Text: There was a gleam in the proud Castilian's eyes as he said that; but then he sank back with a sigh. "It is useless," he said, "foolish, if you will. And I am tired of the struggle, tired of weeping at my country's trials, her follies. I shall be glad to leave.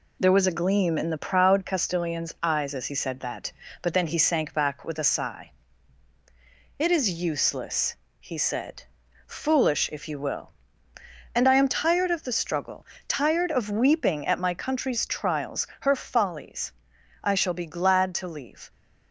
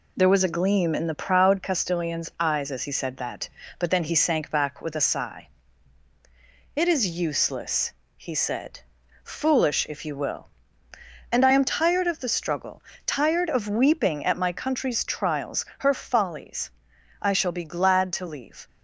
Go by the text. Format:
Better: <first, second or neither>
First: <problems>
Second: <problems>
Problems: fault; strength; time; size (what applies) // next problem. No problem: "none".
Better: neither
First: none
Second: none